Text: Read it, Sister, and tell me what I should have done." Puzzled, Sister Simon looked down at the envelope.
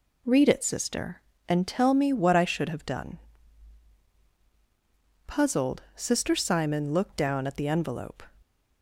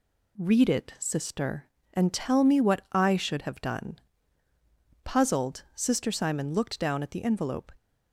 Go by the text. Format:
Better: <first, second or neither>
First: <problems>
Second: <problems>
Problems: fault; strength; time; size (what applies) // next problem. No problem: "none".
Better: neither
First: none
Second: none